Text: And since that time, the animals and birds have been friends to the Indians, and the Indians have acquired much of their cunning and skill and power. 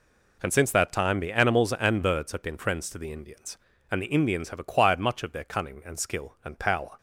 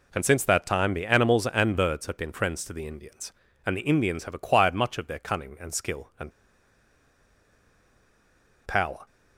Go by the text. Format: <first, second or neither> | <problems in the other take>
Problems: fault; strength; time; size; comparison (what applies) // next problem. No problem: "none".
first | pauses between "and" and "power"; strong; at 6.3 s; 2.3 s long